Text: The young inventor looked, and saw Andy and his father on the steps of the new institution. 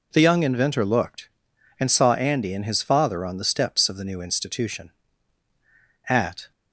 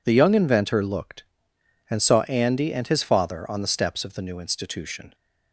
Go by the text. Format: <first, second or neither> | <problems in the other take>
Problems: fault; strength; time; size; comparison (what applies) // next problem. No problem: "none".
second | goes on to say "At"; slight; from 6.0 s on; 0.42 s long